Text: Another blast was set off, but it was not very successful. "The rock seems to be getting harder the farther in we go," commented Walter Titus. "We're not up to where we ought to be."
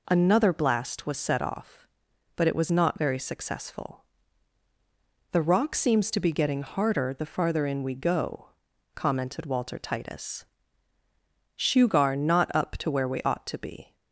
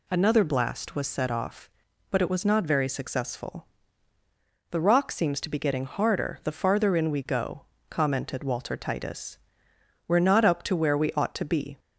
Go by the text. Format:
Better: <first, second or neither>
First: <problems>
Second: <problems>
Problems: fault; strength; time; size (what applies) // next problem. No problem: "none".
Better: second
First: says "Shugar" for "We're"; at 11.5 s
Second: none